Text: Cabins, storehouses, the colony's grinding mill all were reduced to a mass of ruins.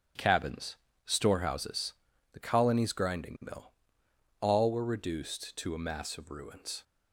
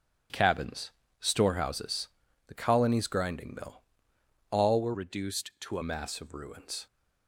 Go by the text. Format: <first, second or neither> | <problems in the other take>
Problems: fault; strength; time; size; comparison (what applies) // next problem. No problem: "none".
first | starts louder than the rest; strong; until 1.5 s; 7 dB; strong in the first // pauses between "mill" and "all"; noticeable; at 3.8 s; 0.68 s long; noticeable in the first // changes voice from "reduced" to "a"; from 4.9 to 5.8 s; 0.9 s long